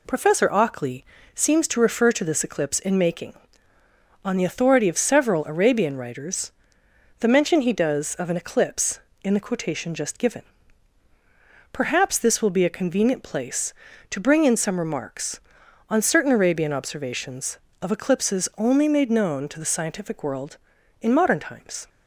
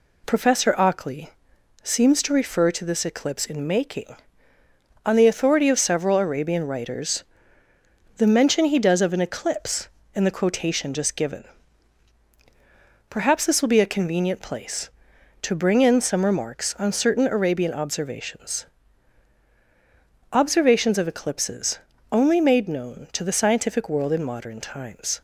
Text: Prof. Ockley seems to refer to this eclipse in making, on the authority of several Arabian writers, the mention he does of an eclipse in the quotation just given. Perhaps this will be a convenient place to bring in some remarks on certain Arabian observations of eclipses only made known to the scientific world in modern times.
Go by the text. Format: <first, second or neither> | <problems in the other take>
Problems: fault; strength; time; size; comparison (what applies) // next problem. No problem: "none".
first | pauses between "Ockley" and "seems"; noticeable; at 1.2 s; 0.54 s long; slight in the first // says "observations" twice; at 20.3 s // pauses between "eclipses" and "only"; slight; at 21.7 s; 0.34 s long